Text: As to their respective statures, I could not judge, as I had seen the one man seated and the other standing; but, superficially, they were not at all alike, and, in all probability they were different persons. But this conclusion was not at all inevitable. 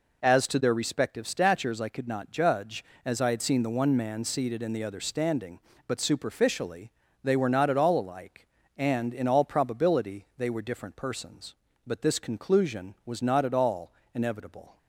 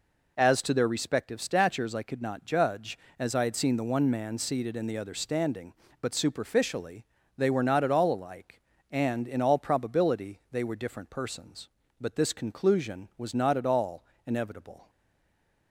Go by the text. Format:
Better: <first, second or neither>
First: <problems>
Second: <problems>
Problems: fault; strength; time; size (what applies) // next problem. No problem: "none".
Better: first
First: pauses between "all" and "inevitable"; slight; at 13.9 s; 0.22 s long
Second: pauses between "all" and "inevitable"; slight; at 14.0 s; 0.22 s long // stays silent after the last word; slight; from 14.8 s on; 0.8 s long